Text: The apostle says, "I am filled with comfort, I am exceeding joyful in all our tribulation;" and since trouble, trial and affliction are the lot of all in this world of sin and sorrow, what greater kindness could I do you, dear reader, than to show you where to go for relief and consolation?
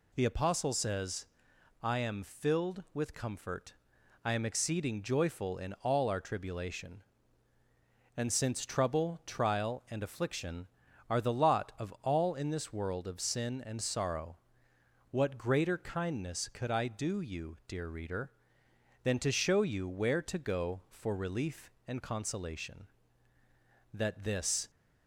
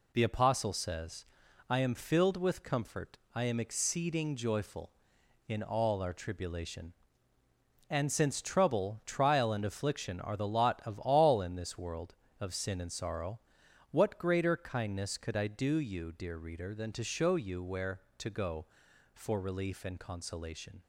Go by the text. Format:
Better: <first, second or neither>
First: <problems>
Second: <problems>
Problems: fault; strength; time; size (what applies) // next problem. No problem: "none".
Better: second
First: goes on to say "That this"; noticeable; from 23.9 s on; 0.76 s long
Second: none